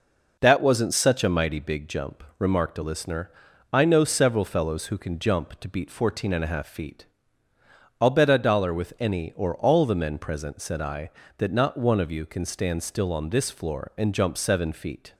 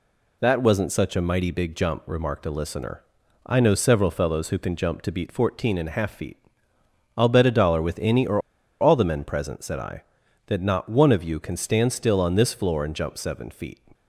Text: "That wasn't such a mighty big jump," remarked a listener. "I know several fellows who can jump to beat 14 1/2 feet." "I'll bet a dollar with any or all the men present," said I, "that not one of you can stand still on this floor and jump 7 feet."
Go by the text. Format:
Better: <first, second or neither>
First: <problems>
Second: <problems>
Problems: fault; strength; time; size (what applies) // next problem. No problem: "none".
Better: first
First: none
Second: pauses between "or" and "all"; at 8.3 s; 0.41 s long